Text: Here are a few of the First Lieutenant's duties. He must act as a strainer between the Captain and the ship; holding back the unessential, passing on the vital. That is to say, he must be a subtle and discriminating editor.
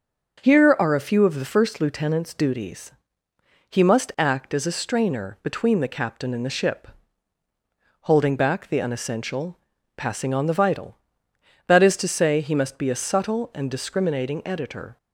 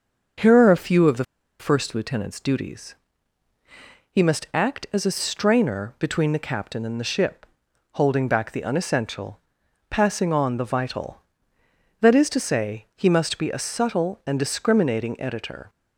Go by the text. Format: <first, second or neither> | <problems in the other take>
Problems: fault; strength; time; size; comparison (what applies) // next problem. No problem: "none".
first | starts louder than the rest; until 1.7 s; 6.5 dB; also in the first // pauses between "the" and "First"; slight; at 1.2 s; 0.34 s long